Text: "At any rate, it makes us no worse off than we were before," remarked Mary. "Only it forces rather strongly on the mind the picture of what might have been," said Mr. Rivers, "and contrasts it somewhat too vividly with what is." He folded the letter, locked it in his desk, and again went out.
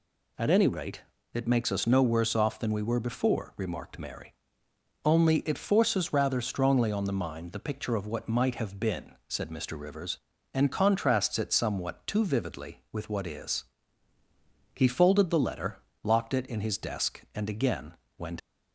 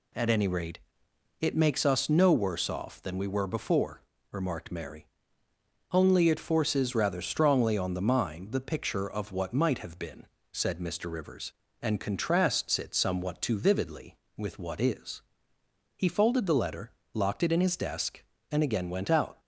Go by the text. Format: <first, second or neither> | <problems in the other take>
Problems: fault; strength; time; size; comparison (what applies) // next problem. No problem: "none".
second | pauses between "again" and "went"; slight; at 17.9 s; 0.24 s long // stops before "out"; at 18.3 s